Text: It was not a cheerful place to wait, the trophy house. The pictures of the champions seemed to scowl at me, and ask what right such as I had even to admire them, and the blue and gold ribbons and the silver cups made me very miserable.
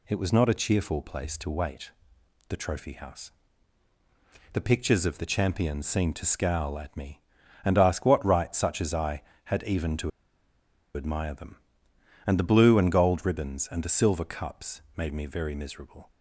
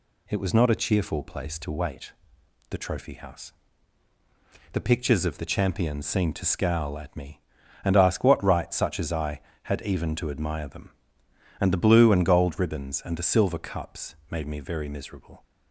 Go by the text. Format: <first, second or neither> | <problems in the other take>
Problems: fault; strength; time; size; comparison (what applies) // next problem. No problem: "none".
second | pauses between "to" and "admire"; noticeable; at 10.1 s; 0.85 s long